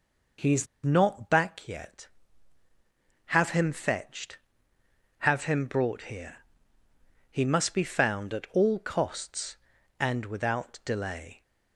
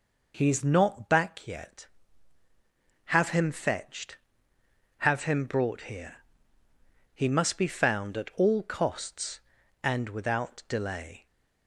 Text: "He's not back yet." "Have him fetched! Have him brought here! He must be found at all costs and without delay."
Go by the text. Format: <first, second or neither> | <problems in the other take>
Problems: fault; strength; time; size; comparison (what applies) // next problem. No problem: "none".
second | pauses between "He's" and "not"; slight; at 0.6 s; 0.19 s long